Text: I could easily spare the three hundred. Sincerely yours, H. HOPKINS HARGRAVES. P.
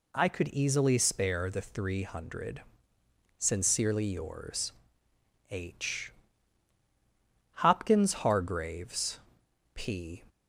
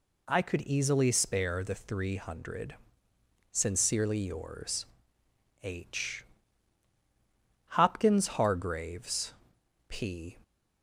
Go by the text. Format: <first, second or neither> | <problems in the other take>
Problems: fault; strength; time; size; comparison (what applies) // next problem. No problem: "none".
neither | none